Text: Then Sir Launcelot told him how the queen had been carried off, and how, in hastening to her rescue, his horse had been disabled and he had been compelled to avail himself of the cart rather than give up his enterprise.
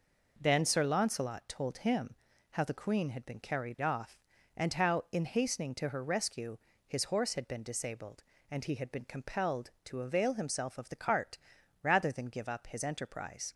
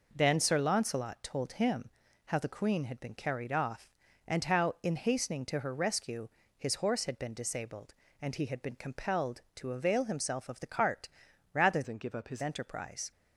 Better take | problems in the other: first | pauses between "him" and "how"; slight; at 1.8 s; 0.36 s long; slight in the first // pauses between "cart" and "rather"; noticeable; at 11.0 s; 0.46 s long; noticeable in the first // changes voice from "than" to "his"; from 11.8 to 12.4 s; 0.6 s long

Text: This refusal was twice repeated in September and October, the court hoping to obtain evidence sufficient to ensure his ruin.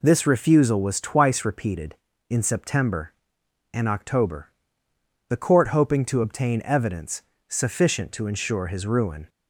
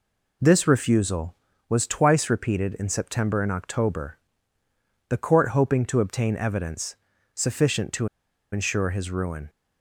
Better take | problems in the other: first | pauses between "evidence" and "sufficient"; at 6.9 s; 0.40 s long; slight in the first // pauses between "to" and "ensure"; at 8.0 s; 0.44 s long

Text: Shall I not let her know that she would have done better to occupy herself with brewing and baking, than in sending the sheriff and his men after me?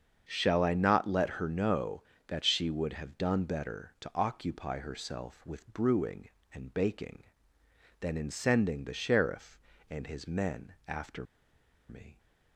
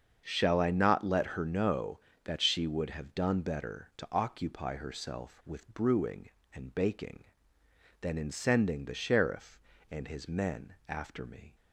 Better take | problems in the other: second | starts louder than the rest; until 1.2 s; 7 dB; also in the second // pauses between "after" and "me"; noticeable; at 11.2 s; 0.64 s long

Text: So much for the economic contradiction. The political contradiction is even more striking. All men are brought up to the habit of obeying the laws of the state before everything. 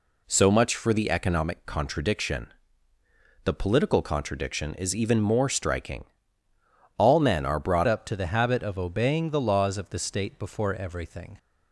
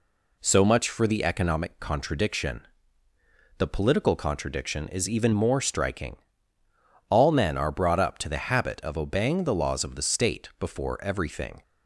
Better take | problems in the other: second | changes voice at "up"; from 7.8 s on; 3.5 s long

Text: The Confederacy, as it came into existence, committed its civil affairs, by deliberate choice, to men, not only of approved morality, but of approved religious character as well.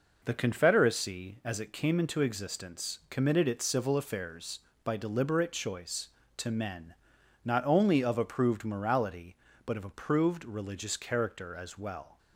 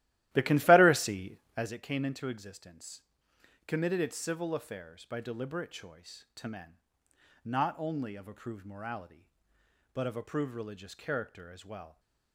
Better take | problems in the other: first | starts louder than the rest; strong; until 1.7 s; 15 dB

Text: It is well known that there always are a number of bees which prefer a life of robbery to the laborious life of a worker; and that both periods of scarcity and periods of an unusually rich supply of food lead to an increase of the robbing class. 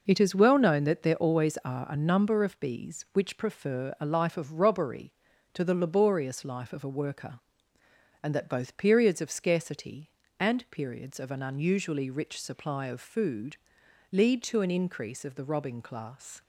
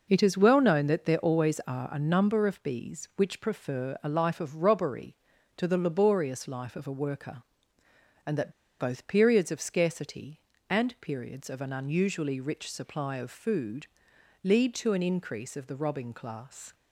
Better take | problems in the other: first | pauses between "that" and "both"; slight; at 8.5 s; 0.28 s long // pauses between "food" and "lead"; noticeable; at 13.8 s; 0.58 s long; noticeable in the first

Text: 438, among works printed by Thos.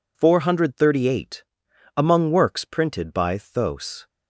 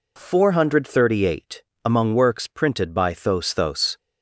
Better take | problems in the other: first | says "Thos" twice; at 3.5 s

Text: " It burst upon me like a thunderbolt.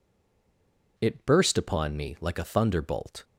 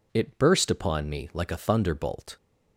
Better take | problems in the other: second | stays silent before the first word; until 0.9 s; 0.9 s long

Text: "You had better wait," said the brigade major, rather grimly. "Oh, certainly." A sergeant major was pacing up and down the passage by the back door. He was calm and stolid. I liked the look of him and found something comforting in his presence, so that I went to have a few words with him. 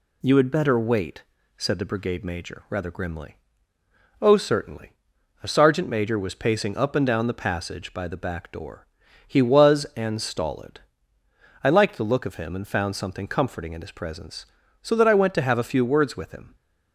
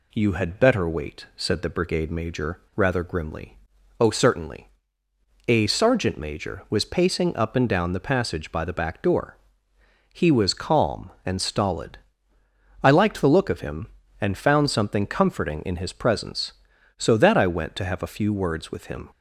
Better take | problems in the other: second | skips "calm"; at 9.8 s

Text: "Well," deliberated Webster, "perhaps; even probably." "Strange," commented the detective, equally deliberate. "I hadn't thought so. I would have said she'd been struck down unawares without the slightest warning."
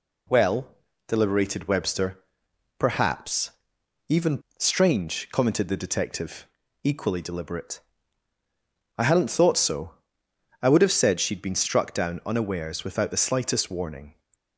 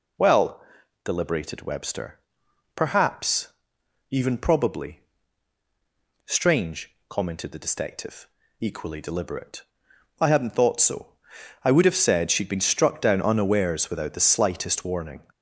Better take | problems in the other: second | skips "probably"; at 4.4 s

